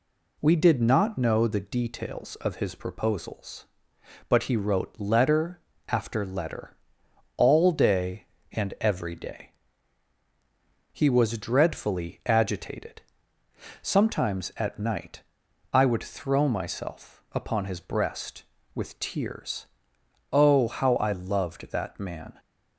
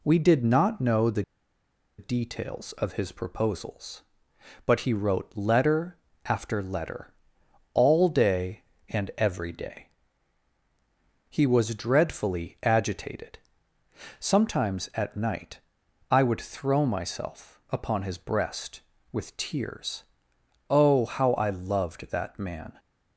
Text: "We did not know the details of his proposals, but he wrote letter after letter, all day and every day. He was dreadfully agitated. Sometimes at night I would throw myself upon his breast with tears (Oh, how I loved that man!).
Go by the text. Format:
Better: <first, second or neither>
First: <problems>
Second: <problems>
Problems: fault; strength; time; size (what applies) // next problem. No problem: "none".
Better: first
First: pauses between "letter" and "after"; slight; at 5.5 s; 0.28 s long // pauses between "night" and "I"; noticeable; at 15.2 s; 0.52 s long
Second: pauses between "the" and "details"; noticeable; at 1.2 s; 0.75 s long // pauses between "letter" and "after"; slight; at 5.9 s; 0.28 s long // pauses between "night" and "I"; noticeable; at 15.5 s; 0.52 s long